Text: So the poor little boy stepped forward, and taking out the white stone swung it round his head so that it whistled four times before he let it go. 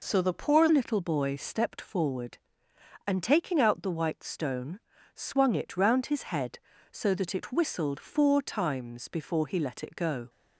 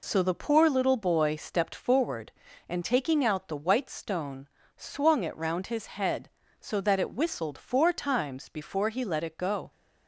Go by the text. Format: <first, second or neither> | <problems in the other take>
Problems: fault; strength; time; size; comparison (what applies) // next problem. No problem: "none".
second | changes voice at "little"; from 0.7 s on; 9.5 s long // pauses between "stone" and "swung"; at 4.7 s; 0.38 s long; slight in the second